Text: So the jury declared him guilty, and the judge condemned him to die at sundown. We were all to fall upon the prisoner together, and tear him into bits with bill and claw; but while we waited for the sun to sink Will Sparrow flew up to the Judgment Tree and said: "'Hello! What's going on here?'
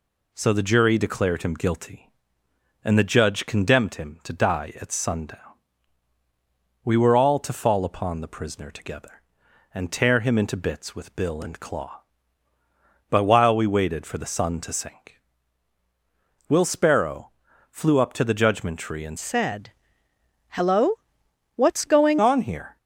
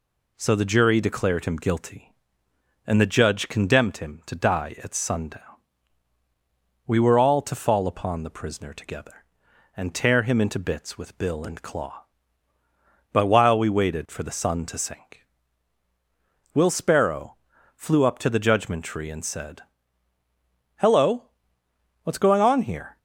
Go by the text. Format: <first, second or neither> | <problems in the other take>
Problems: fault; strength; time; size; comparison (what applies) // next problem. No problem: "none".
second | pauses between "Sparrow" and "flew"; at 17.3 s; 0.40 s long; also in the second // changes voice from "said" to "going"; from 19.1 to 22.1 s; 3.0 s long